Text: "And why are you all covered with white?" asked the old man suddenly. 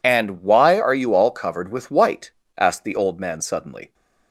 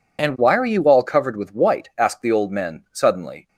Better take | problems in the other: first | says "men" for "man"; at 2.5 s

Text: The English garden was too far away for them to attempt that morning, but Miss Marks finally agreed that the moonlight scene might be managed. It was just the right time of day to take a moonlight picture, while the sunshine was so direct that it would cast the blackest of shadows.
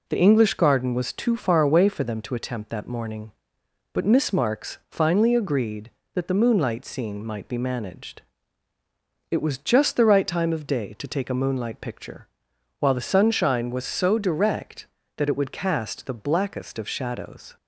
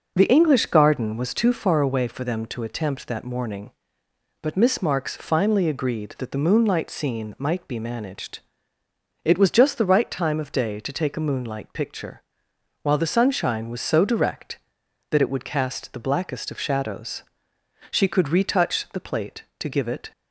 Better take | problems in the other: first | goes on to say "She could retouch the plate to give it"; strong; from 17.8 s on; 2.2 s long

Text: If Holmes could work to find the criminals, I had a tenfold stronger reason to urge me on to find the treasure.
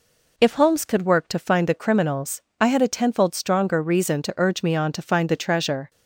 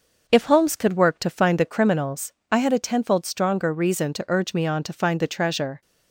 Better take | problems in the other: first | starts louder than the rest; noticeable; until 2.1 s; 6 dB

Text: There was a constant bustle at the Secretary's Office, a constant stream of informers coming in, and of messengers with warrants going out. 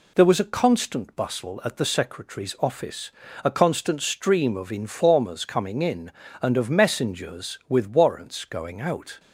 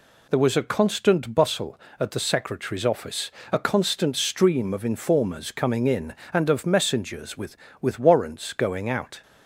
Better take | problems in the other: first | says "with" twice; at 7.7 s

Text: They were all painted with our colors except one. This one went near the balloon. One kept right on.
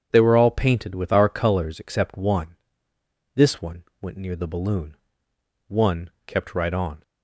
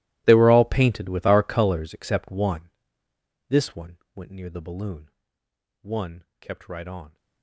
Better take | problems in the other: first | gets quieter; strong; throughout; 21 dB // starts louder than the rest; strong; until 1.2 s; 17 dB; strong in the first // pauses between "one" and "went"; slight; at 3.9 s; 0.16 s long; slight in the first // pauses between "One" and "kept"; slight; at 6.2 s; 0.16 s long; slight in the first

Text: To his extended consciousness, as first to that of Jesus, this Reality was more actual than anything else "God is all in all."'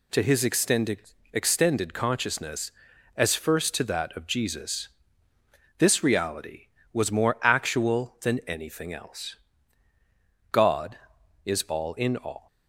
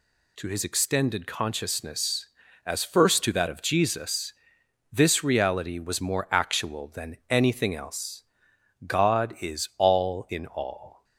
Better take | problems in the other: second | says "extended" twice; at 1.3 s // pauses between "else" and "God"; at 9.3 s; 1.1 s long; noticeable in the second

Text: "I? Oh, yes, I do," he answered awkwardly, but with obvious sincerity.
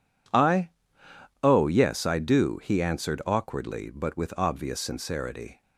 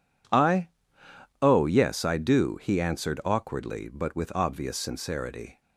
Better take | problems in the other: neither | none

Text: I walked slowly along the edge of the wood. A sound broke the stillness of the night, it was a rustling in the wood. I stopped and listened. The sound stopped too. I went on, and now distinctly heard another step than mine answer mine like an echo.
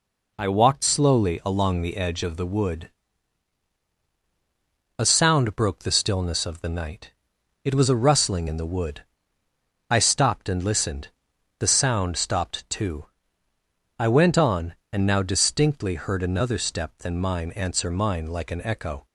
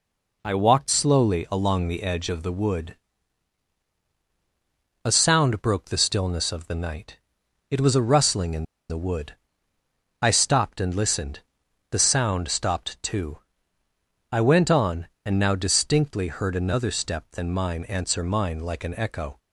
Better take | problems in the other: first | pauses between "in" and "the"; slight; at 8.6 s; 0.26 s long

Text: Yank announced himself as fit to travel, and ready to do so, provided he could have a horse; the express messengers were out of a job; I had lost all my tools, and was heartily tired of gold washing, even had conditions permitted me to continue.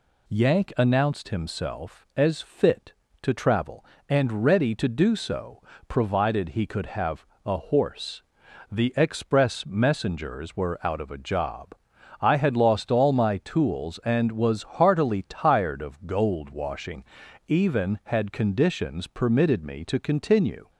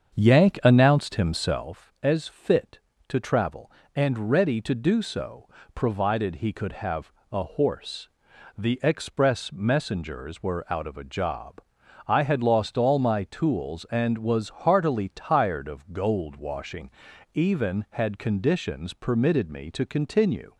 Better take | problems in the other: first | starts louder than the rest; strong; until 1.7 s; 7 dB // pauses between "have" and "a"; slight; at 7.1 s; 0.18 s long; slight in the first

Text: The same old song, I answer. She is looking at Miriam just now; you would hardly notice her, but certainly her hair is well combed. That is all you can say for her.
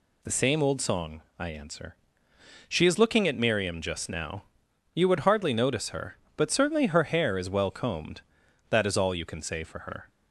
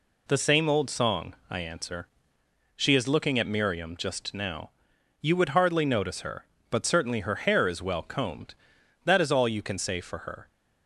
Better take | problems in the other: neither | none

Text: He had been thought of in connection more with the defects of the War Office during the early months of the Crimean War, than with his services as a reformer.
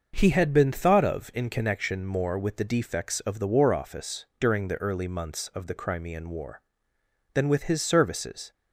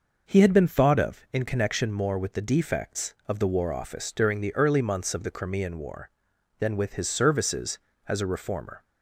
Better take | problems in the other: second | starts louder than the rest; noticeable; until 1.1 s; 6 dB // stops before "as a reformer"; at 8.5 s

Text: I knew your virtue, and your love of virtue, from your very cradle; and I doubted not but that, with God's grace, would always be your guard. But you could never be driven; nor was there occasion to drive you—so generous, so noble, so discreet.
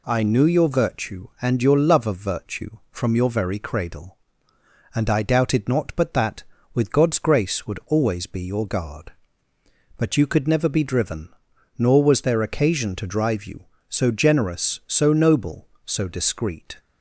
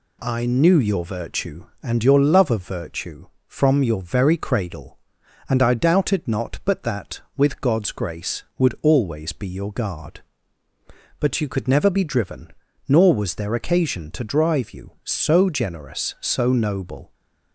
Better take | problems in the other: first | stops before "so discreet"; at 17.1 s

